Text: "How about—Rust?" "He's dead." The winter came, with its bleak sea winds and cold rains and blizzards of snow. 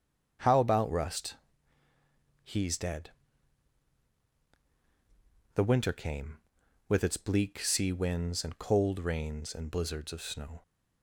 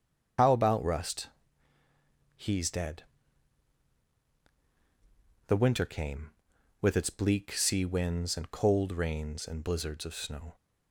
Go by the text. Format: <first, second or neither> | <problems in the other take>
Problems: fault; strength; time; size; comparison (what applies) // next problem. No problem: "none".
first | loses the start of "How"; at 0.3 s; 55 ms // starts louder than the rest; strong; until 2.4 s; 7.5 dB; strong in the first